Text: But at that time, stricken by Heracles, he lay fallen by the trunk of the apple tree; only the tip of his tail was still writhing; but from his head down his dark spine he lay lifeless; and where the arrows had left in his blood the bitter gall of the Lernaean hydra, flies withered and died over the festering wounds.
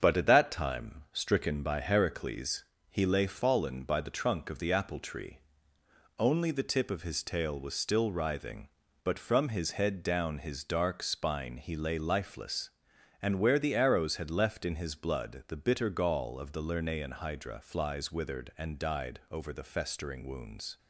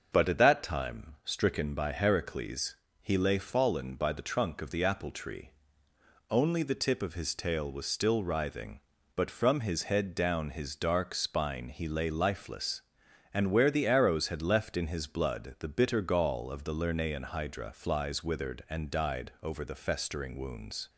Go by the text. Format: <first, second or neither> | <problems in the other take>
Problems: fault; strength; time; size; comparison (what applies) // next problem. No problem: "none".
second | gets quieter; noticeable; throughout; 5 dB // starts louder than the rest; until 1.0 s; 7 dB; also in the second